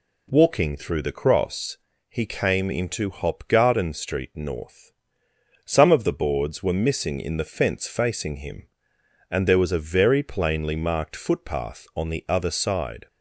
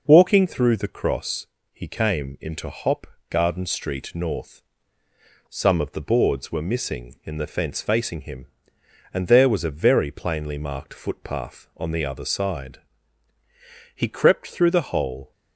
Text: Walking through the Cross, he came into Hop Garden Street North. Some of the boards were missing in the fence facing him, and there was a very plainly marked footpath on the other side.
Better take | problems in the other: first | pauses between "Hop" and "Garden"; slight; at 3.0 s; 0.24 s long // goes on to say "He crept through the hole"; from 13.9 s on; 1.3 s long

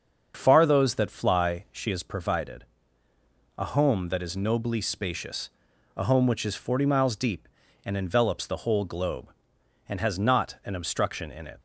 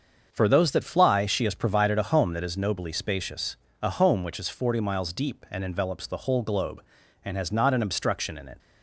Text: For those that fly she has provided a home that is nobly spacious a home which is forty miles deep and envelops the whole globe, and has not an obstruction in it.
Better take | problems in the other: second | starts louder than the rest; until 1.3 s; 7 dB; also in the second // says "Far" for "For"; at 0.3 s // pauses between "provided" and "a"; noticeable; at 2.6 s; 0.92 s long // pauses between "spacious" and "a"; noticeable; at 5.4 s; 0.46 s long; slight in the second

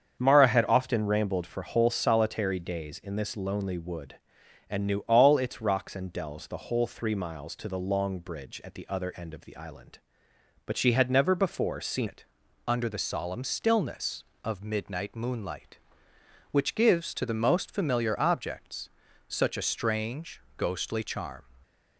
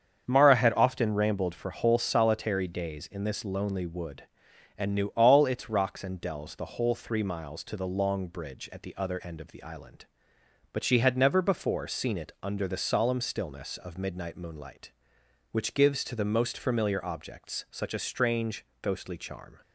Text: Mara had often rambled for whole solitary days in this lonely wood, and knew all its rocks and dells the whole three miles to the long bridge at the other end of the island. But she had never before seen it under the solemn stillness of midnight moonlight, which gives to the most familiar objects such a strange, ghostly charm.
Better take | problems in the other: second | starts louder than the rest; strong; until 1.2 s; 7.5 dB; strong in the second // changes voice at "it"; from 12.0 s on; 9.4 s long // pauses between "it" and "under"; at 12.2 s; 0.42 s long // pauses between "objects" and "such"; at 18.8 s; 0.40 s long

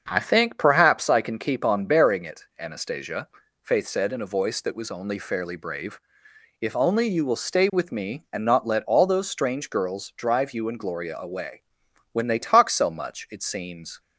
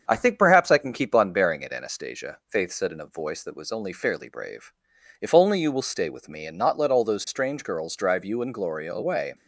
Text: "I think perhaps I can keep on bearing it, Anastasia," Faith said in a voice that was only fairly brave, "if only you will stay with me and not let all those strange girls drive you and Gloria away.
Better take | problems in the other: second | starts louder than the rest; until 1.0 s; 7 dB; strong in the second // goes on to say "When they talk so much it seems"; strong; from 12.1 s on; 1.8 s long

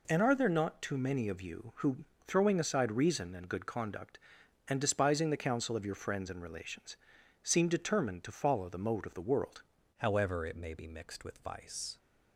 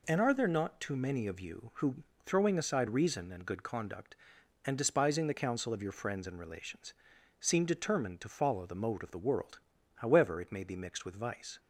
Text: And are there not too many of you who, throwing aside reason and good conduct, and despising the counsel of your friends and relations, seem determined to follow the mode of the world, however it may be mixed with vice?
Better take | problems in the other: second | changes voice at "however"; from 9.9 s on; 2.0 s long

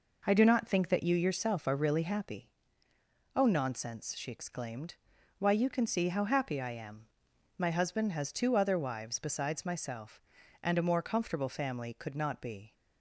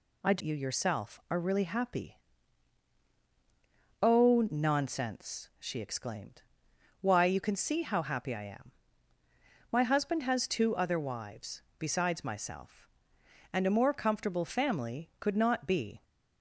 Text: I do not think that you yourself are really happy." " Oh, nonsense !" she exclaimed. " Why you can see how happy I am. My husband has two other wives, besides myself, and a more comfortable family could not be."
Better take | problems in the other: first | skips "not think that"; at 0.4 s

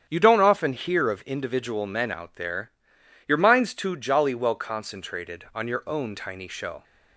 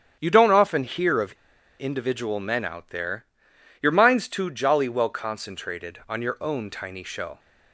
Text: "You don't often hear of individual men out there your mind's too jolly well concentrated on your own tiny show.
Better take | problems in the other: first | starts louder than the rest; strong; until 1.2 s; 9 dB; strong in the first // pauses between "of" and "individual"; noticeable; at 1.3 s; 0.47 s long // pauses between "there" and "your"; noticeable; at 3.2 s; 0.56 s long; noticeable in the first

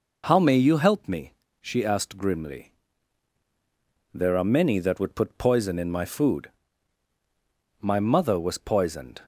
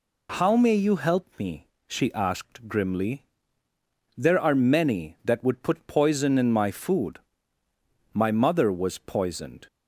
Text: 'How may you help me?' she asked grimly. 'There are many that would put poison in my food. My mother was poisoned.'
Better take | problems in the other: neither | none

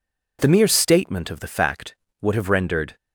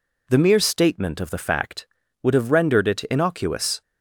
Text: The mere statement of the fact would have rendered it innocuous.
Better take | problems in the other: second | stops before "it innocuous"; at 2.9 s

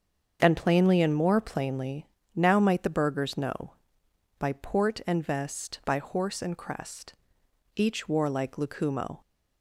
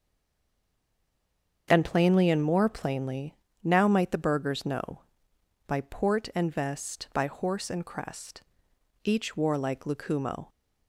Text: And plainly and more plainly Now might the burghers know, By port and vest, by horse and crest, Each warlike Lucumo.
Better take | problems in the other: first | stays silent before the first word; noticeable; until 1.6 s; 1.6 s long // starts louder than the rest; until 2.6 s; 7 dB; also in the first // pauses between "plainly" and "Now"; slight; at 3.3 s; 0.28 s long; slight in the first

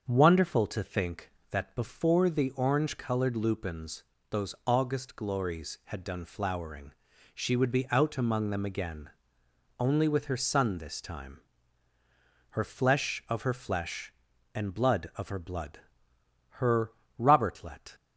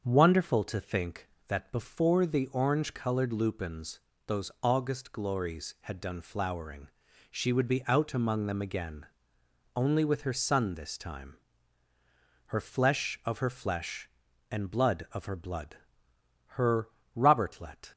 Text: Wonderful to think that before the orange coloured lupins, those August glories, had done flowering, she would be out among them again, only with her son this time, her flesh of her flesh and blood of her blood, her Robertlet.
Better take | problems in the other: neither | starts louder than the rest; the same in both // pauses between "her" and "Robertlet"; slight; the same in both

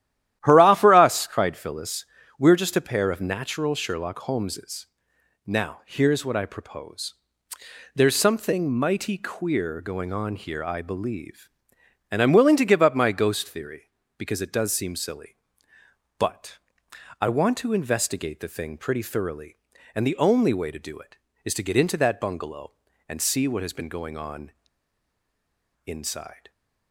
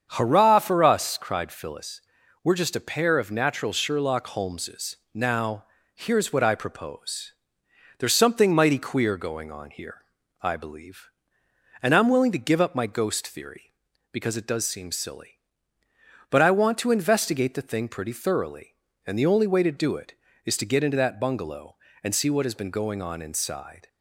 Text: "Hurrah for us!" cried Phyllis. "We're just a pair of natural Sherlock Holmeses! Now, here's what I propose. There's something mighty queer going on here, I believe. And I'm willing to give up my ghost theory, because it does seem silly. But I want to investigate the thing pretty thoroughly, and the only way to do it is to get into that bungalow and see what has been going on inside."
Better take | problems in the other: second | starts louder than the rest; strong; until 1.4 s; 12.5 dB; strong in the second // pauses between "But" and "I"; noticeable; at 16.5 s; 0.62 s long // pauses between "on" and "inside"; strong; at 24.5 s; 1.3 s long

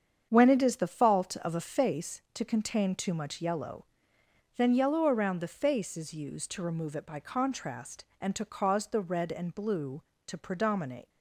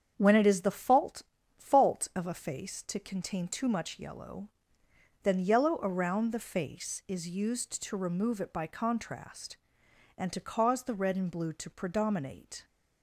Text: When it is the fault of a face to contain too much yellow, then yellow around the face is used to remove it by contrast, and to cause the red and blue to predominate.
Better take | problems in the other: first | starts louder than the rest; strong; until 1.1 s; 8 dB; strong in the first // says "fault" twice; at 1.5 s

